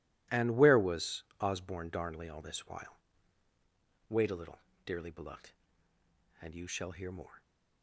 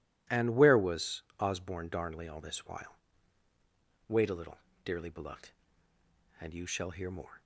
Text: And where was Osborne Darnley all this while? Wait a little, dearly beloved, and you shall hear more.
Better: second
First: gets quieter; strong; throughout; 14 dB // pauses between "was" and "Osborne"; slight; at 1.2 s; 0.18 s long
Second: pauses between "was" and "Osborne"; slight; at 1.2 s; 0.18 s long

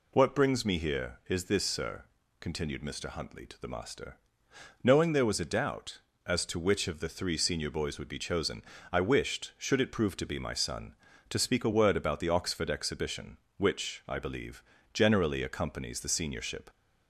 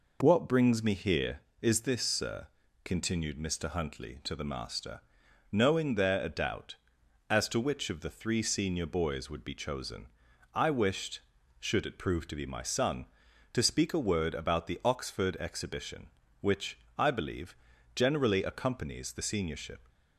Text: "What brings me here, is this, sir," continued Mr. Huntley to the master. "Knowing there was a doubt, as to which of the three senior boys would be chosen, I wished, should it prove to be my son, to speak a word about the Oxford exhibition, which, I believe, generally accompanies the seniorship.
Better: first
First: none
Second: skips "was"; at 6.2 s

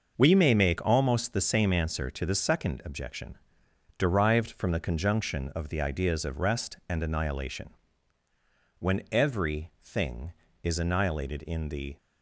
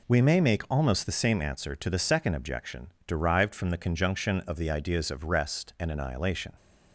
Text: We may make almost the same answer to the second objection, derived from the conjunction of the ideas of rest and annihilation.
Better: second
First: starts louder than the rest; noticeable; until 1.1 s; 6 dB // goes on to say "When every thing is annihilated in the"; strong; from 8.7 s on; 3.1 s long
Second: none

